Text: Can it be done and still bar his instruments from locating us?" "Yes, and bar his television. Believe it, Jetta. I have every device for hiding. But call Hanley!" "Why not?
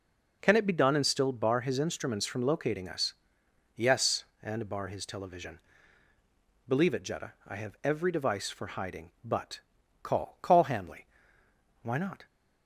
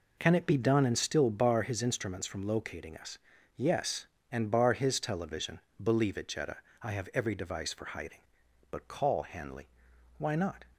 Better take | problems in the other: second | pauses between "But" and "call"; at 9.6 s; 0.42 s long // says "call" twice; at 10.3 s

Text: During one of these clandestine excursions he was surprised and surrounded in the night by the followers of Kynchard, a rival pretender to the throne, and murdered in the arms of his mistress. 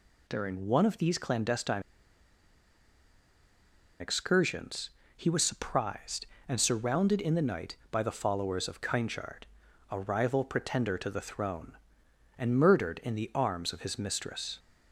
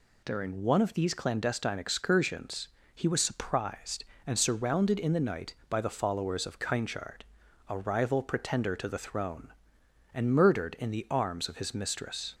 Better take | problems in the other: second | pauses between "clandestine" and "excursions"; strong; at 1.8 s; 2.1 s long // pauses between "excursions" and "he"; slight; at 4.9 s; 0.26 s long; slight in the second

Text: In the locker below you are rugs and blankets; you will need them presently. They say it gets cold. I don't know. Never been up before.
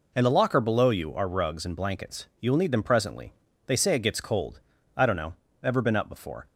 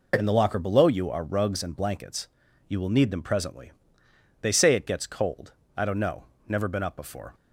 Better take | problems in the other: second | says "Ever" for "Never"; at 5.6 s

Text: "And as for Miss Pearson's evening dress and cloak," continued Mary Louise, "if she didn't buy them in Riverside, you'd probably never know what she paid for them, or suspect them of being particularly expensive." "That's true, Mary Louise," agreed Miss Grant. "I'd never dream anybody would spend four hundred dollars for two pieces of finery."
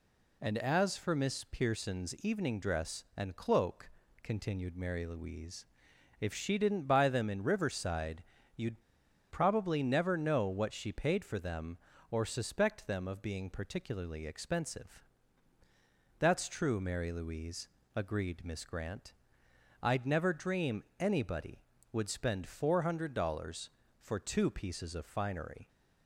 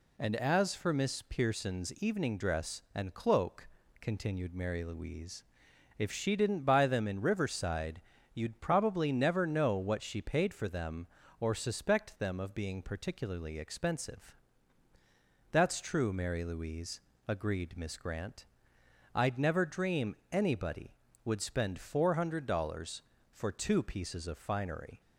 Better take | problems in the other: second | pauses between "you'd" and "probably"; noticeable; at 8.8 s; 0.49 s long // pauses between "dream" and "anybody"; slight; at 20.8 s; 0.16 s long; slight in the second

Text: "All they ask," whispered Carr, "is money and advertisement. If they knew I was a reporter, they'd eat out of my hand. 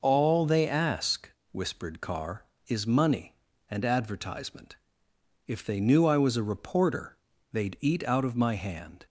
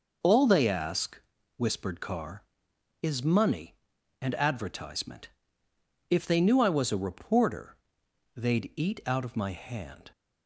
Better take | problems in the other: neither | none

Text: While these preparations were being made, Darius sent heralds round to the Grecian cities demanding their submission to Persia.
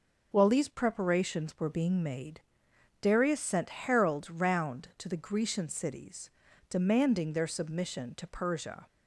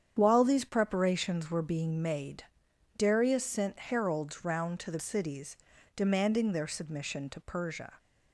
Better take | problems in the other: first | starts louder than the rest; strong; until 1.2 s; 8.5 dB // skips "Grecian"; at 4.9 s // pauses between "cities" and "demanding"; at 5.5 s; 0.40 s long; also in the first

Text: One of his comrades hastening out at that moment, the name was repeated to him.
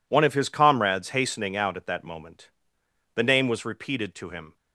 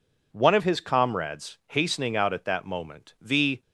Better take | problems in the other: first | stops before "name was repeated to him"; at 3.6 s

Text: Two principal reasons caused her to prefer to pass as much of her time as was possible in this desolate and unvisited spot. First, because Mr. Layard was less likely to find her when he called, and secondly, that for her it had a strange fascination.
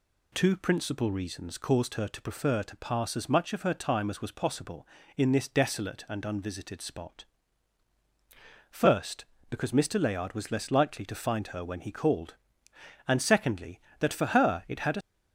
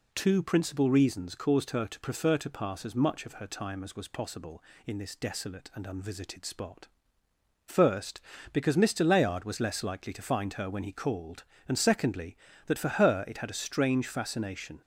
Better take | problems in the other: second | stops before "strange fascination"; at 15.0 s

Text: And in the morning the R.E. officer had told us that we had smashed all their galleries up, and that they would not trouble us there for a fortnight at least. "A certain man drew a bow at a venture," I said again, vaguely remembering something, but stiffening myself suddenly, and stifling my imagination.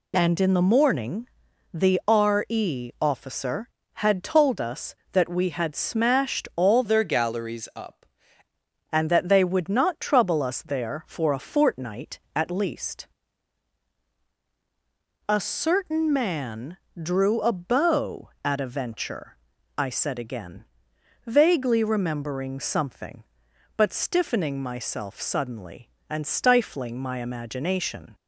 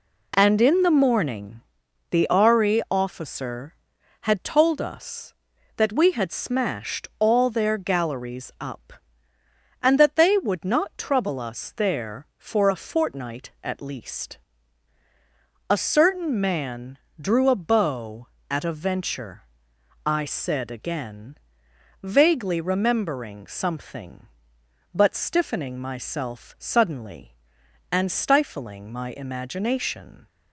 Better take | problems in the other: second | pauses between "morning" and "the"; noticeable; at 1.2 s; 0.46 s long; noticeable in the second // changes voice from "their" to "up"; from 6.8 to 8.0 s; 1.2 s long // pauses between "man" and "drew"; slight; at 16.7 s; 0.22 s long; slight in the second

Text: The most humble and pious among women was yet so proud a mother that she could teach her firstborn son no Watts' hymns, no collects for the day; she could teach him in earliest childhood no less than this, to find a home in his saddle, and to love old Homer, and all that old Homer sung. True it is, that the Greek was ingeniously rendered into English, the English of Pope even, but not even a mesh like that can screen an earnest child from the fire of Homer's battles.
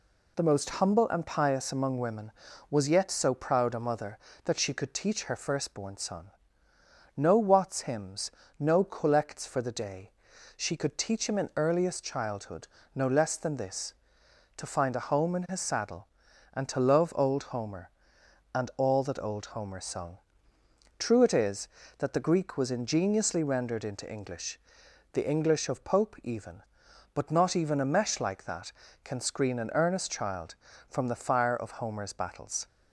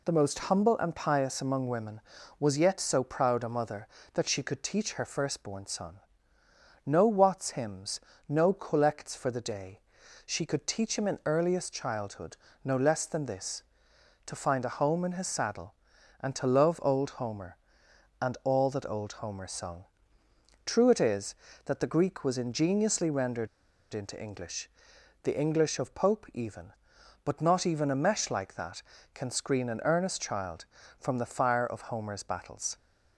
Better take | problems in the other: first | pauses between "son" and "no"; noticeable; at 5.9 s; 0.86 s long; noticeable in the first // pauses between "childhood" and "no"; slight; at 12.3 s; 0.26 s long; slight in the first // pauses between "rendered" and "into"; at 23.4 s; 0.45 s long

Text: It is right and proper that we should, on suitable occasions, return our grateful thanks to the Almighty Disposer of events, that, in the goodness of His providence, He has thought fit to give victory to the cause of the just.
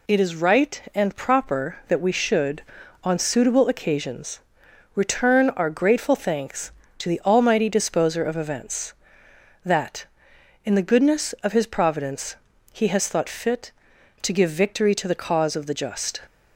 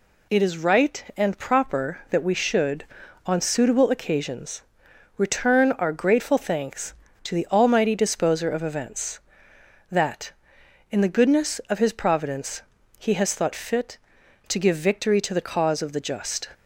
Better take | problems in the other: neither | none

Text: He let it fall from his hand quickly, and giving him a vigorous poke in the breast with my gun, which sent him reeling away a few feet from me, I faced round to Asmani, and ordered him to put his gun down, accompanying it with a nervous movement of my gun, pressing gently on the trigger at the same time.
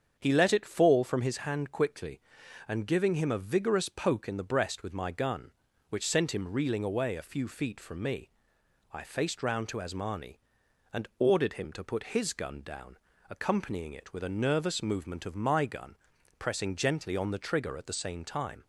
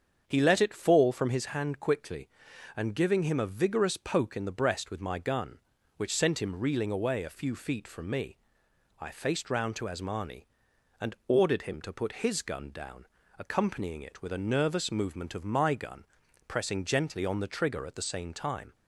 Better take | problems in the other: neither | starts louder than the rest; strong; the same in both

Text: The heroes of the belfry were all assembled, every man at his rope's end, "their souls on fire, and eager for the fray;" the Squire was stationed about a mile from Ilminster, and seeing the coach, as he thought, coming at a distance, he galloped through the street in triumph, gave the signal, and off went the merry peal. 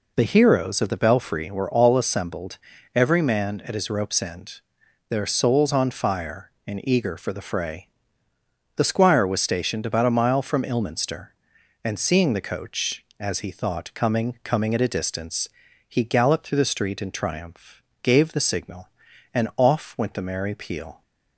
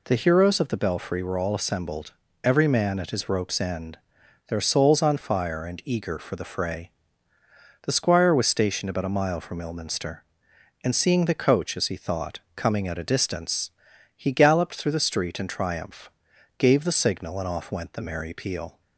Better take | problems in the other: second | says "coming" twice; at 14.4 s

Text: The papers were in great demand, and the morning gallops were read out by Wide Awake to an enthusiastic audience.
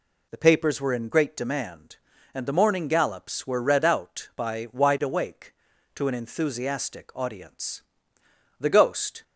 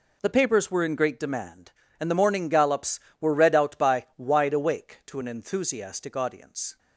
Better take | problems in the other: second | goes on to say "The Ghost"; noticeable; from 8.6 s on; 0.62 s long

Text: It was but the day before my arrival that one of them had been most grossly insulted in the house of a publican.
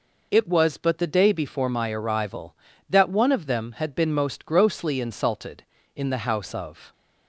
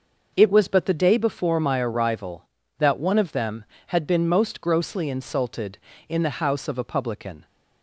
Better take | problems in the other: second | stops before "a publican"; at 6.9 s

